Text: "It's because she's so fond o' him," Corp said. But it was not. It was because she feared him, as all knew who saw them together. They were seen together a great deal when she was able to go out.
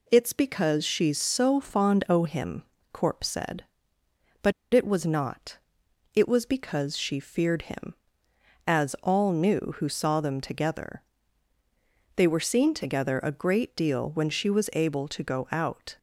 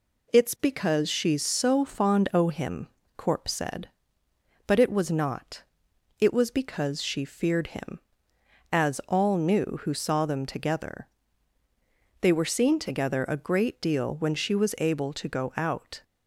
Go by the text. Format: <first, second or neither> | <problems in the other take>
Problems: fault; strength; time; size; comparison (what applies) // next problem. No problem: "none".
second | pauses between "But" and "it"; slight; at 4.5 s; 0.21 s long